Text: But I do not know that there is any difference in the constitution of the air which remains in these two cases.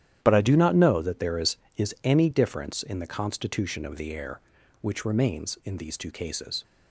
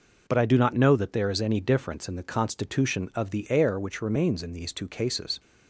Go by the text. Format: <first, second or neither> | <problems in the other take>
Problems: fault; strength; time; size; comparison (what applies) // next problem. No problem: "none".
second | starts louder than the rest; strong; until 1.2 s; 11 dB // says "is" twice; at 1.7 s